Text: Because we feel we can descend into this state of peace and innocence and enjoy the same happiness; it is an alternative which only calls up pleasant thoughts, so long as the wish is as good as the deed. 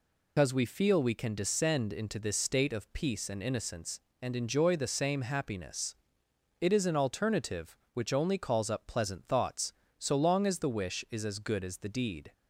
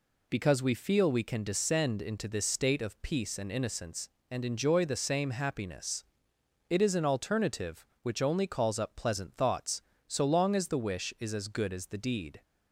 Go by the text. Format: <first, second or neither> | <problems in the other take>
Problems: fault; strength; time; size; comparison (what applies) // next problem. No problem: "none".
second | loses the start of "Because"; at 0.3 s; 155 ms